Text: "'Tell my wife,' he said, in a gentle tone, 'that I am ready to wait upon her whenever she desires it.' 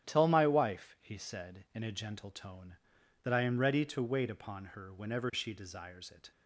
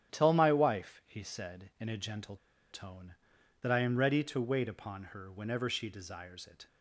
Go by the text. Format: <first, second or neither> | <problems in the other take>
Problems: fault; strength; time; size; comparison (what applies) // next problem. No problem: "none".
first | starts louder than the rest; strong; until 1.1 s; 10 dB; strong in the first // pauses between "gentle" and "tone"; slight; at 2.3 s; 0.35 s long